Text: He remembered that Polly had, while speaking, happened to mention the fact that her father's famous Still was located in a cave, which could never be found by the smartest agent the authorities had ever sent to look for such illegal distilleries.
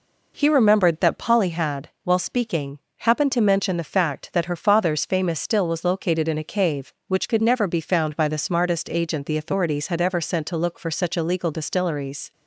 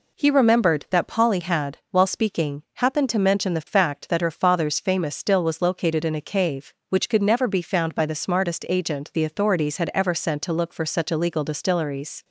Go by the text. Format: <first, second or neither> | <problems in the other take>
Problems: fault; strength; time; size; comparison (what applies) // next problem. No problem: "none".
neither | none